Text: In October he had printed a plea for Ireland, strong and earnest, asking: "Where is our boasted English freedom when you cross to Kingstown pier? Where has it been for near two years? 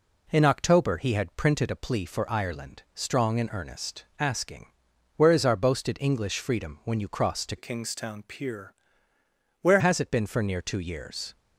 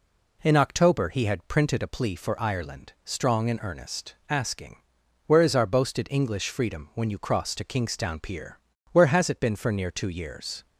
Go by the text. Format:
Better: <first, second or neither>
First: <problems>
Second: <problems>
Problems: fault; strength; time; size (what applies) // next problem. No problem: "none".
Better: second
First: changes voice from "Kingstown" to "Where"; from 7.5 to 9.8 s; 2.3 s long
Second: none